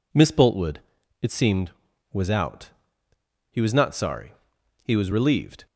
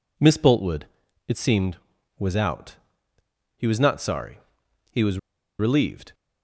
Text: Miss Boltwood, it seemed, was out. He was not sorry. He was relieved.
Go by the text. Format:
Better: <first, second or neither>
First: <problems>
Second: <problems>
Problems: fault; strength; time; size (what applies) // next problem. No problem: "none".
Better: first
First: none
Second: pauses between "was" and "relieved"; at 5.1 s; 0.41 s long